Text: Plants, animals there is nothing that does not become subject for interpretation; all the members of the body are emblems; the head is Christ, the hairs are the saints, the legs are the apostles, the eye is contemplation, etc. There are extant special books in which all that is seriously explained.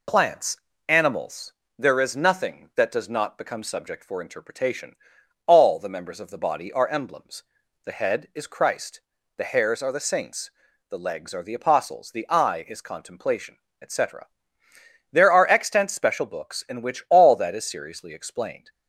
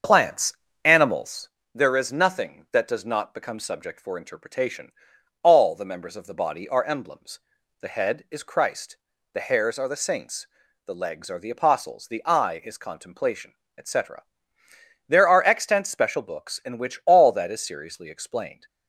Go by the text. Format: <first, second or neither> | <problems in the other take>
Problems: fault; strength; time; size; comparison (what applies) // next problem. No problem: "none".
first | starts louder than the rest; until 1.6 s; 7 dB // pauses between "animals" and "there"; slight; at 1.4 s; 0.24 s long; slight in the first